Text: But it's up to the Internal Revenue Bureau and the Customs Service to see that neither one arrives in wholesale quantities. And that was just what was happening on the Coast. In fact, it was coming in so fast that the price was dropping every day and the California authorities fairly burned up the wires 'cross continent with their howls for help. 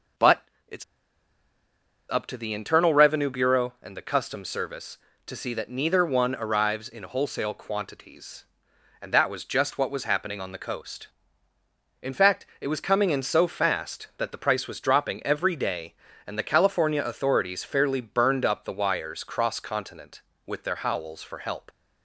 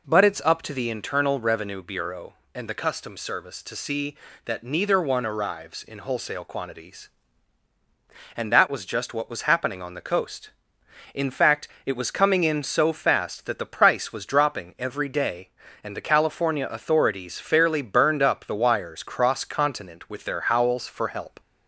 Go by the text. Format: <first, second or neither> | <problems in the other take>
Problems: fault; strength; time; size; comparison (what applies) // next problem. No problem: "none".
second | pauses between "But" and "it's"; slight; at 0.4 s; 0.24 s long // pauses between "it's" and "up"; strong; at 0.8 s; 1.2 s long